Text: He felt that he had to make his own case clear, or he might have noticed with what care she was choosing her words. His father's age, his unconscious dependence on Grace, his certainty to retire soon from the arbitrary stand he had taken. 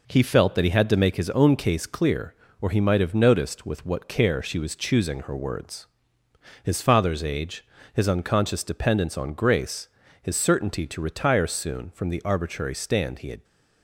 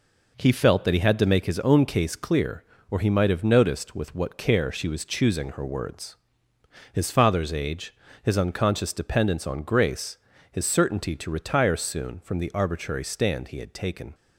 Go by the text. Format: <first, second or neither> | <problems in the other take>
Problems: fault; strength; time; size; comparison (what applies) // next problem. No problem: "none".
second | stops before "taken"; at 13.4 s